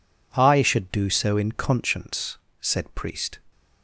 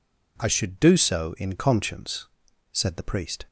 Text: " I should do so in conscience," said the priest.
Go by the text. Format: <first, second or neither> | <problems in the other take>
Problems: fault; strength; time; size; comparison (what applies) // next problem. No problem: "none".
second | skips "the"; at 2.9 s